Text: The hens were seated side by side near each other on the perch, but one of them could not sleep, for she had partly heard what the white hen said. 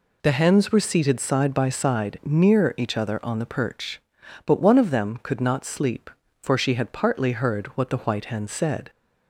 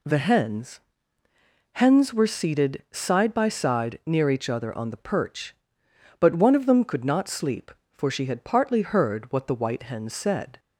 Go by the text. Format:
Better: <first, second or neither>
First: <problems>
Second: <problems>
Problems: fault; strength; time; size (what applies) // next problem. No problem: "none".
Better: first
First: none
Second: says "hens" twice; at 1.7 s